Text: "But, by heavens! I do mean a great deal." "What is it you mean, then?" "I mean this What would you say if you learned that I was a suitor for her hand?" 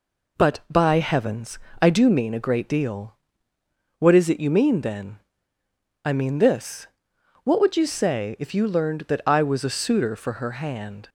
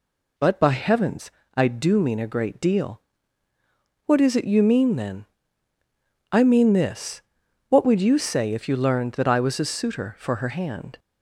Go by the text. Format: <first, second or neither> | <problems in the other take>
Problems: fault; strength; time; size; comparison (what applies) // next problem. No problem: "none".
neither | pauses between "this" and "What"; noticeable; the same in both